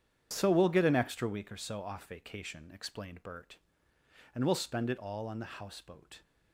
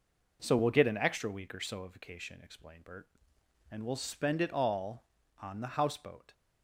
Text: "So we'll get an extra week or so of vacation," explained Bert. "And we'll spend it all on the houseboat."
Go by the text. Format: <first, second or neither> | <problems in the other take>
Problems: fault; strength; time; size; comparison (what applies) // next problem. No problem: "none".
second | starts louder than the rest; strong; until 1.3 s; 8.5 dB // says "off" for "of"; at 1.8 s